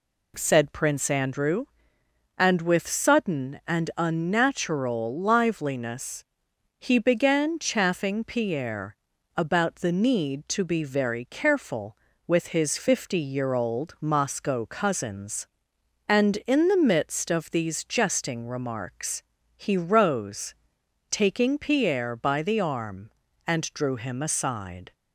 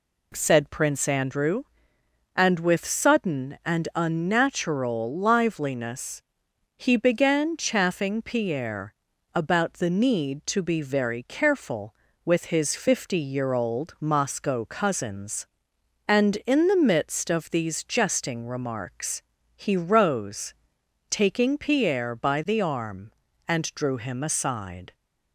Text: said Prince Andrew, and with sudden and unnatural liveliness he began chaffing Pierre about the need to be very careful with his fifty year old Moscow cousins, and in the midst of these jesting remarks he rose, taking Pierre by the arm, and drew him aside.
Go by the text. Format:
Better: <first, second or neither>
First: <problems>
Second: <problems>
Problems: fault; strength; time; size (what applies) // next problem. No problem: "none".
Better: neither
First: pauses between "liveliness" and "he"; noticeable; at 6.2 s; 0.56 s long // pauses between "Pierre" and "about"; at 8.9 s; 0.42 s long // pauses between "remarks" and "he"; slight; at 19.2 s; 0.34 s long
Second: pauses between "liveliness" and "he"; noticeable; at 6.2 s; 0.56 s long // pauses between "Pierre" and "about"; at 8.9 s; 0.42 s long // pauses between "remarks" and "he"; slight; at 19.2 s; 0.34 s long